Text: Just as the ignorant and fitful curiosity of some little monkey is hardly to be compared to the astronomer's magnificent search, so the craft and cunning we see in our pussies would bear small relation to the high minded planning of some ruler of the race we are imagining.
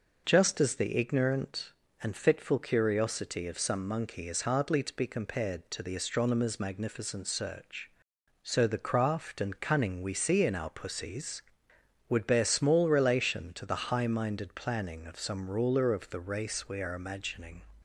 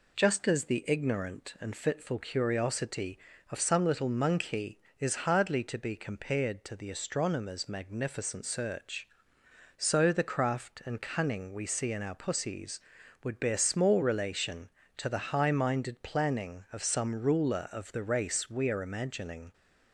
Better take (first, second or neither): second